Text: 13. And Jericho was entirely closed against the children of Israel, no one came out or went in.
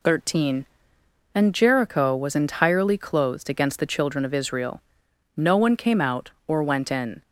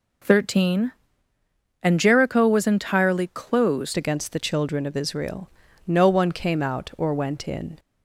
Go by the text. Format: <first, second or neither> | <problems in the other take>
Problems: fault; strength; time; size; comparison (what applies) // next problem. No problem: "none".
first | changes voice at "against"; from 3.9 s on; 3.8 s long